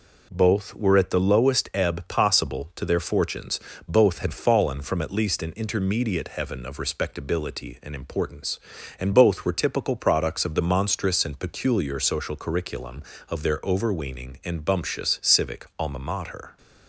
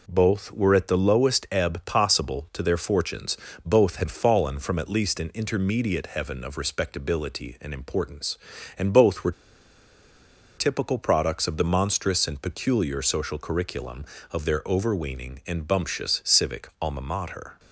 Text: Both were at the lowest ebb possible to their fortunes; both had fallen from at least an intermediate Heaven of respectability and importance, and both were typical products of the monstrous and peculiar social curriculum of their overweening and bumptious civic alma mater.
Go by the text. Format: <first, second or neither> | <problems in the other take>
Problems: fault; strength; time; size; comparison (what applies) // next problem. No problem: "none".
first | pauses between "were" and "typical"; strong; at 9.3 s; 1.2 s long